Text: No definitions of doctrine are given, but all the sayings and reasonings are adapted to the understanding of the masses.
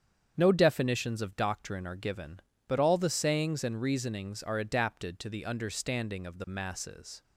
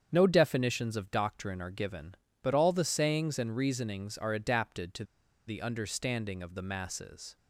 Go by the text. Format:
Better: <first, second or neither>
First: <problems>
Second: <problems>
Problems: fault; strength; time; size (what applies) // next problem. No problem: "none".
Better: first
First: starts louder than the rest; strong; until 1.3 s; 8 dB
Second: starts louder than the rest; strong; until 1.1 s; 7.5 dB // pauses between "to" and "the"; at 5.0 s; 0.44 s long